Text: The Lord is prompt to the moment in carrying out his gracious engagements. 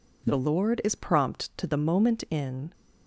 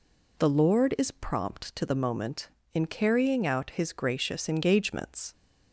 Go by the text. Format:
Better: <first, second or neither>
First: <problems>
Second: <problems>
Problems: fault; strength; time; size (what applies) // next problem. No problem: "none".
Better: second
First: stops before "carrying out his gracious engagements"; at 2.7 s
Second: none